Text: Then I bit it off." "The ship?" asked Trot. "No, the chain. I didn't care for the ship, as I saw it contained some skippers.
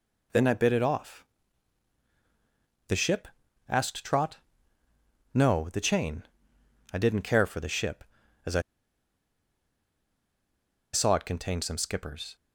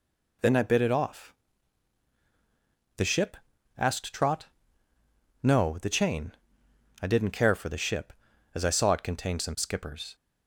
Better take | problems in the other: second | pauses between "I" and "saw"; strong; at 8.5 s; 2.3 s long

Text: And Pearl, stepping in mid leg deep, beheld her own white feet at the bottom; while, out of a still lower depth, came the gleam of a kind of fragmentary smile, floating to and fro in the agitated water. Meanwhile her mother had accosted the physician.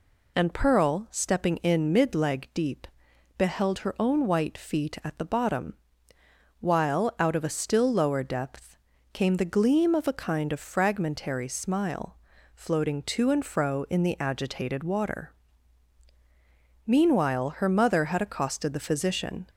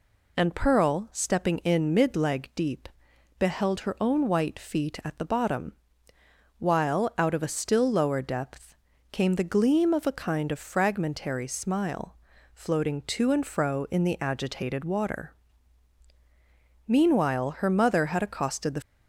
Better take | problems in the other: first | stops before "physician"; at 18.8 s

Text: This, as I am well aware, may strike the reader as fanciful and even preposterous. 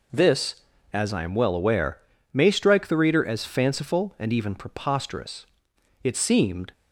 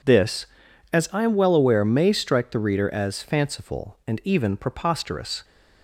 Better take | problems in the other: second | goes on to say "It seemed"; noticeable; from 6.0 s on; 0.68 s long

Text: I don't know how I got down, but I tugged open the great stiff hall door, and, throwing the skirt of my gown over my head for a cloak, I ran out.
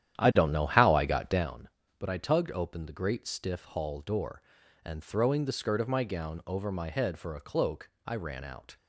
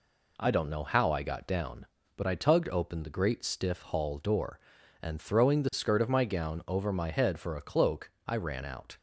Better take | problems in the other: second | starts louder than the rest; strong; until 1.5 s; 10.5 dB

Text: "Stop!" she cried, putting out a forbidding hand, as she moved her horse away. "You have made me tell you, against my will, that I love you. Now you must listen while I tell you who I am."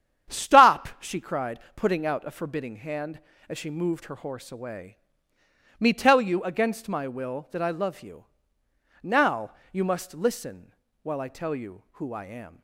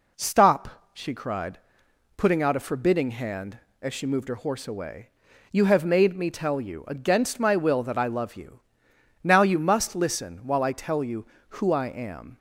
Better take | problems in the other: second | starts louder than the rest; strong; until 1.3 s; 9 dB // skips "You have made"; at 5.3 s // pauses between "Now" and "you"; slight; at 9.5 s; 0.18 s long // pauses between "listen" and "while"; slight; at 10.7 s; 0.28 s long

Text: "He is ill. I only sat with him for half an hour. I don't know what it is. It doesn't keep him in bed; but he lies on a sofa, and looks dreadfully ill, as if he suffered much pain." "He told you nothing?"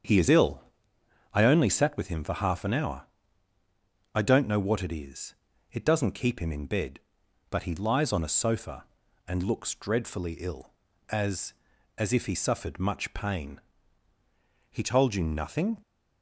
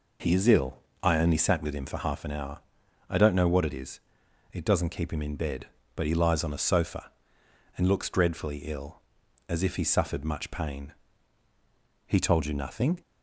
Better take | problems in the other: second | starts louder than the rest; strong; until 1.7 s; 7.5 dB // says "as" twice; at 11.9 s

